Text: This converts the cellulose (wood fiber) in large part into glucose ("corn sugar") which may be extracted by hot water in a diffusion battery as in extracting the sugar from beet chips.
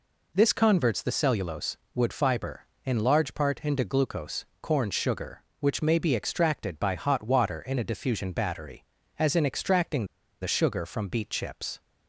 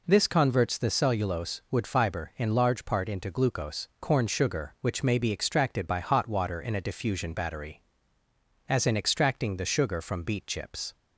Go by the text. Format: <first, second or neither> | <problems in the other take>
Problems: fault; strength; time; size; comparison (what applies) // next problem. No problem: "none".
second | pauses between "extracting" and "the"; at 10.0 s; 0.36 s long